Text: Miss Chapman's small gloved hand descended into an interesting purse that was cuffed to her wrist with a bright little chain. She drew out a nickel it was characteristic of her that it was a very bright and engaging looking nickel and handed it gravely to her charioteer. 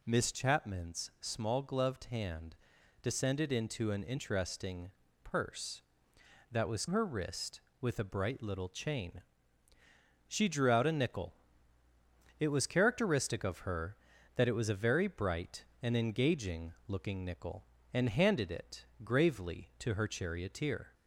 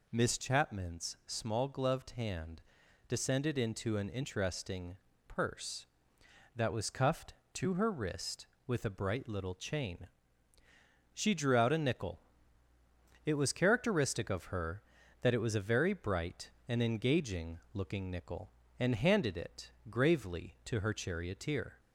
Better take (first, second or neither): second